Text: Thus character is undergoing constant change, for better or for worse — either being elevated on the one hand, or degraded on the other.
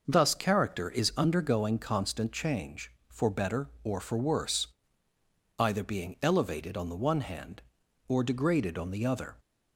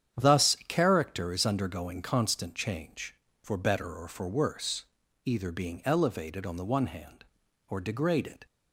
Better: first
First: none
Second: starts louder than the rest; strong; until 1.2 s; 9 dB // stops before "on the other"; at 8.4 s

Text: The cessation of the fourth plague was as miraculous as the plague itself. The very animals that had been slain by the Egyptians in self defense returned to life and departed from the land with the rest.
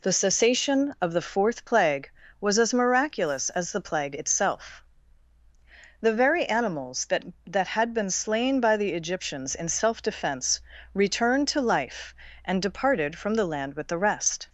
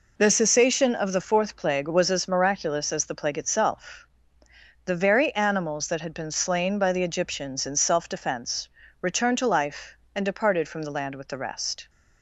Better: second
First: says "that" twice; at 7.4 s // pauses between "defense" and "returned"; slight; at 10.5 s; 0.34 s long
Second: pauses between "defense" and "returned"; slight; at 8.6 s; 0.32 s long

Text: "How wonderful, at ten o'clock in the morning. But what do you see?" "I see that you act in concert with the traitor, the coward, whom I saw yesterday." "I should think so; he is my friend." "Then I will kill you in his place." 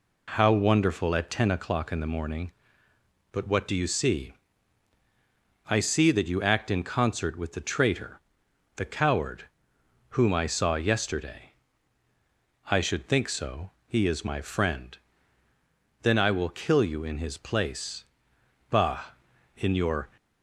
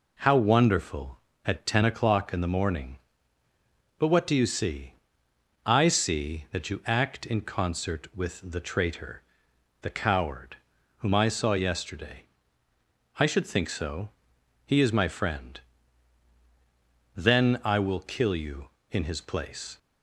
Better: second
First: goes on to say "Bah in your"; from 18.6 s on; 1.4 s long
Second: none

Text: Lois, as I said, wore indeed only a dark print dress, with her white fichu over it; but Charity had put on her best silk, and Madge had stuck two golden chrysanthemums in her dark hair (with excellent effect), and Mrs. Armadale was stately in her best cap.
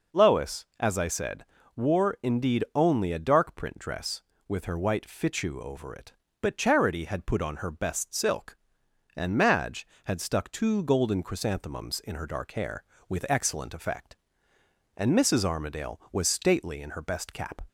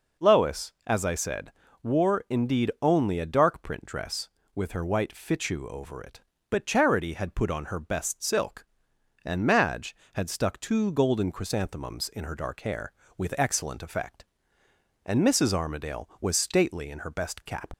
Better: first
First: none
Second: leaves "cap" unfinished; at 17.7 s; 65 ms

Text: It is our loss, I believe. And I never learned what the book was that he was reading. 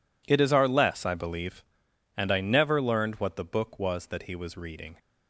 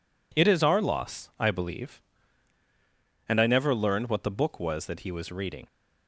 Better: second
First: says "less" for "loss"; at 0.6 s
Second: none

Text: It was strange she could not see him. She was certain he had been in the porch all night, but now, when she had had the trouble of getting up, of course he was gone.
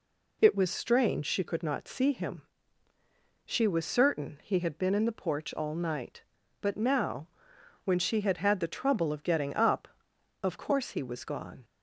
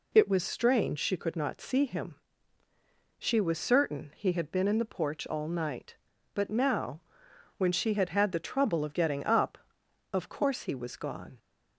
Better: neither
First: none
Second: none

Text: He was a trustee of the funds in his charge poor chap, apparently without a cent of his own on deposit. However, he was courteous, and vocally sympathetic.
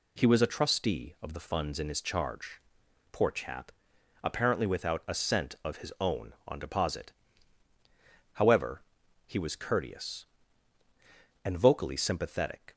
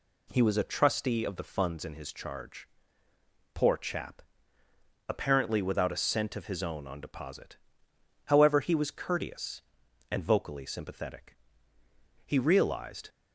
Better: first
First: pauses between "charge" and "poor"; noticeable; at 2.5 s; 0.52 s long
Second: pauses between "charge" and "poor"; noticeable; at 2.6 s; 0.88 s long // goes on to say "He realized"; noticeable; from 12.2 s on; 0.84 s long

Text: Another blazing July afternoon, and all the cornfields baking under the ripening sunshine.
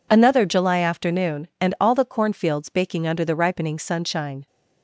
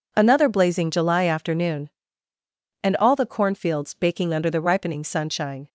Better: second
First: skips "blazing"; at 0.4 s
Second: none

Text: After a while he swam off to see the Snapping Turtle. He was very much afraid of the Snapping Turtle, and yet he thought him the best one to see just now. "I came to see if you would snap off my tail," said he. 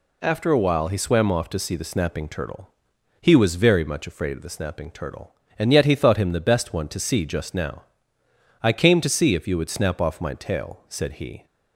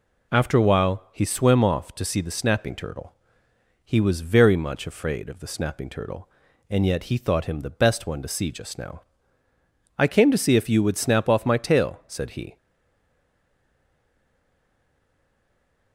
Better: first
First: none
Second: stays silent after the last word; strong; from 12.5 s on; 3.4 s long

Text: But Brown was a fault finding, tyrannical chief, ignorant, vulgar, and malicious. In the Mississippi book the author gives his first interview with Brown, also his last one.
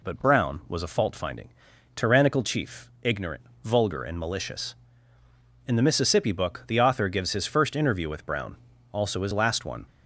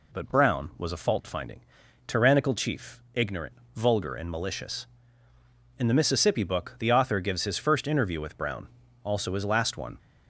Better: neither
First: none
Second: none

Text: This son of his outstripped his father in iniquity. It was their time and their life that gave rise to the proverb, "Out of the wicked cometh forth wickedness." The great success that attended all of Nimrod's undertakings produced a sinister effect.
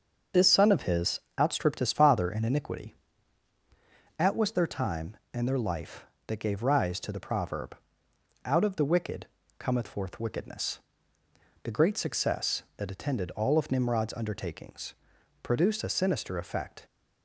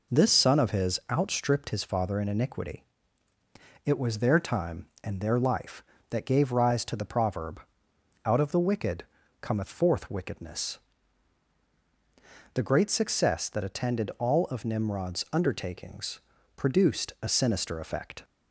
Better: second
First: starts louder than the rest; until 1.5 s; 6.5 dB // pauses between "his" and "outstripped"; slight; at 1.2 s; 0.18 s long // says "At" for "It"; at 4.1 s // pauses between "wicked" and "cometh"; slight; at 9.2 s; 0.32 s long // pauses between "undertakings" and "produced"; noticeable; at 14.9 s; 0.48 s long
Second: pauses between "wicked" and "cometh"; at 9.0 s; 0.38 s long // pauses between "undertakings" and "produced"; slight; at 16.1 s; 0.36 s long

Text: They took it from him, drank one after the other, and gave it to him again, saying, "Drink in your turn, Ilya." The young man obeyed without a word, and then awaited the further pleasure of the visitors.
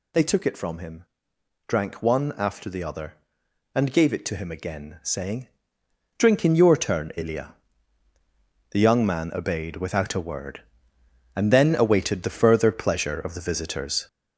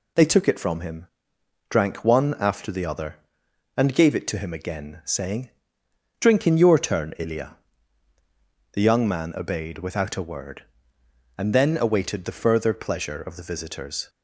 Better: second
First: gets louder; noticeable; throughout; 5.5 dB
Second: none

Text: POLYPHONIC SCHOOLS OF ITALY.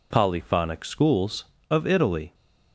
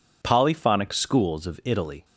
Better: neither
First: none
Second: none

